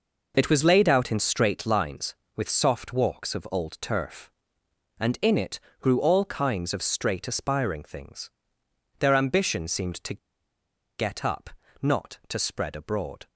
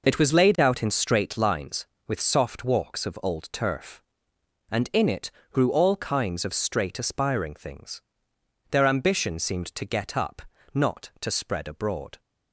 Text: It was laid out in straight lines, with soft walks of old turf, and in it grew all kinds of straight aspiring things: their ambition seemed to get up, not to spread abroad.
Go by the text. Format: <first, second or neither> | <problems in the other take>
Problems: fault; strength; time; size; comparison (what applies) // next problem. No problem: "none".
second | pauses between "it" and "grew"; slight; at 5.5 s; 0.20 s long; slight in the second // pauses between "to" and "get"; noticeable; at 10.1 s; 0.81 s long